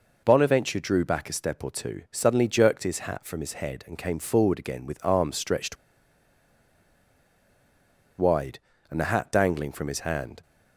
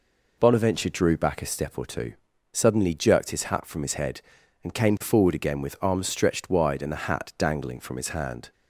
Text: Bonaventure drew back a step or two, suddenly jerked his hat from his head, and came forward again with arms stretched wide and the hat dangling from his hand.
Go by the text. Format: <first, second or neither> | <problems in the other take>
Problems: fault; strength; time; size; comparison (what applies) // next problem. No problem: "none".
second | pauses between "stretched" and "wide"; strong; at 5.7 s; 2.4 s long